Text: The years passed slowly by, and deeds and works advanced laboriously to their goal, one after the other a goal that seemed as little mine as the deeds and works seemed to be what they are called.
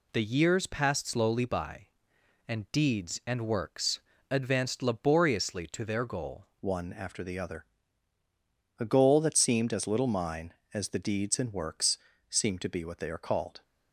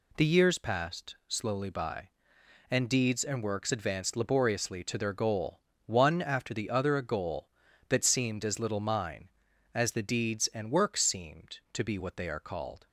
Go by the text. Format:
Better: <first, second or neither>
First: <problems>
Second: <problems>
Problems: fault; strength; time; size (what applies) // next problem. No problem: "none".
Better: second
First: pauses between "works" and "advanced"; slight; at 3.9 s; 0.32 s long // changes voice at "one"; from 6.6 s on; 7.0 s long // pauses between "other" and "a"; at 7.6 s; 1.1 s long // pauses between "works" and "seemed"; slight; at 11.9 s; 0.32 s long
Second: none